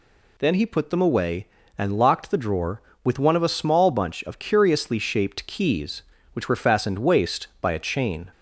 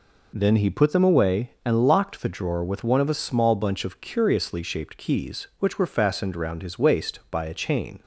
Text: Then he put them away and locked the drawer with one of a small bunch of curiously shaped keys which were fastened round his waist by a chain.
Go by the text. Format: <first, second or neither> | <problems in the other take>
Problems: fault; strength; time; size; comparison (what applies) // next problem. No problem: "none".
second | skips "round his"; at 6.9 s